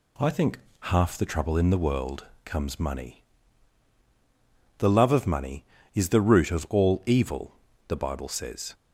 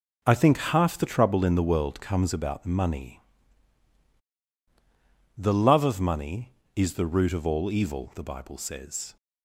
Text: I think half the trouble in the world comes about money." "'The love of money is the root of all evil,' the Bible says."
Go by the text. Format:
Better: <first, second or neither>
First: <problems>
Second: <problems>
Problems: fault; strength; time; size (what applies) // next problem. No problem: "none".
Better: second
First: pauses between "think" and "half"; slight; at 0.5 s; 0.20 s long // pauses between "world" and "comes"; slight; at 2.2 s; 0.18 s long // skips "about"; at 2.7 s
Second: none